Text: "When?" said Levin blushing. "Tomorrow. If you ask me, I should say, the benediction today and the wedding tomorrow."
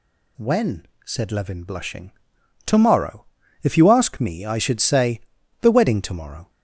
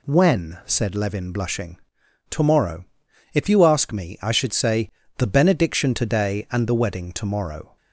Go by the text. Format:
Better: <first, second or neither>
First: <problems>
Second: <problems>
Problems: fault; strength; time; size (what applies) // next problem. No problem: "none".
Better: second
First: skips "benediction today and the"; at 5.7 s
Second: none